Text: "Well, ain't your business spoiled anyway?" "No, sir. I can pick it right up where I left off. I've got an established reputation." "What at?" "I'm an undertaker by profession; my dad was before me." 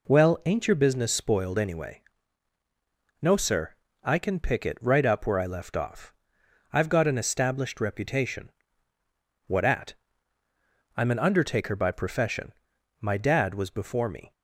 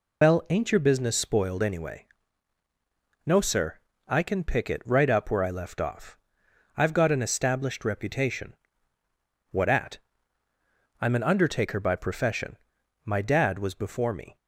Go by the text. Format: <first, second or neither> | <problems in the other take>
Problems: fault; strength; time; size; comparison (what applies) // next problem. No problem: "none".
first | loses the start of "Well"; at 0.2 s; 110 ms